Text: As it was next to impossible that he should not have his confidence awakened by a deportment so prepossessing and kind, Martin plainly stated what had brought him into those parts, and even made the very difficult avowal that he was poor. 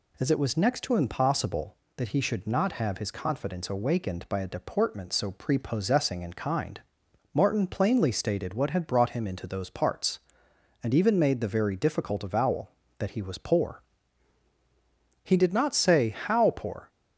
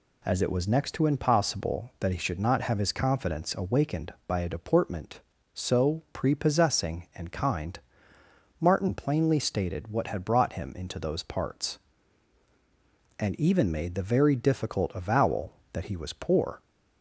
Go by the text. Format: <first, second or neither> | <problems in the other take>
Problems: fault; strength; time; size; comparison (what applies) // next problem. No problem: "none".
second | goes on to say "He did not say how poor"; from 15.2 s on; 1.6 s long